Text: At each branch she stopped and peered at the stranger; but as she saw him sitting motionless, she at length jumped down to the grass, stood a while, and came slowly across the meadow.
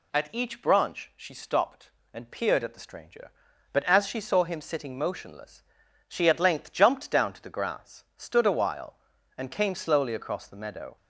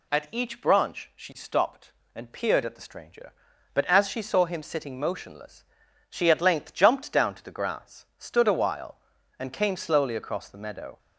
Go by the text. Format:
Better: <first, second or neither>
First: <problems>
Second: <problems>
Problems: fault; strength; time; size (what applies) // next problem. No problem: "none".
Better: neither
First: none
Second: none